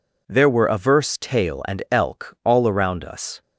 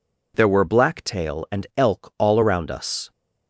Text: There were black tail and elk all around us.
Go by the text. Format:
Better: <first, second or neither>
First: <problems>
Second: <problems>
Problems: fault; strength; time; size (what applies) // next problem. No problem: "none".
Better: second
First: says "averse" for "black"; at 0.6 s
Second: none